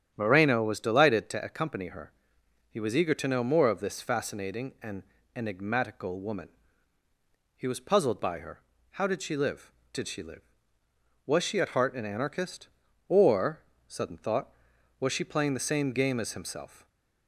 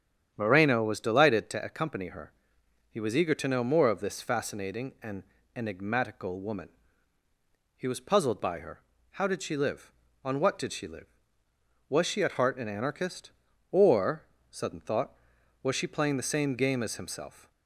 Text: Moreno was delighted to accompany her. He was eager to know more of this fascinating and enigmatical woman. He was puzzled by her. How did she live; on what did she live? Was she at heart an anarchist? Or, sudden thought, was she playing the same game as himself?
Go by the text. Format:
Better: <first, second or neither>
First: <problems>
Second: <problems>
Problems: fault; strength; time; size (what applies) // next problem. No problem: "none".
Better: second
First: starts louder than the rest; strong; until 1.1 s; 9 dB // pauses between "and" and "enigmatical"; slight; at 5.0 s; 0.32 s long // skips "on what"; at 9.8 s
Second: starts louder than the rest; strong; until 1.3 s; 9 dB // pauses between "and" and "enigmatical"; slight; at 5.2 s; 0.32 s long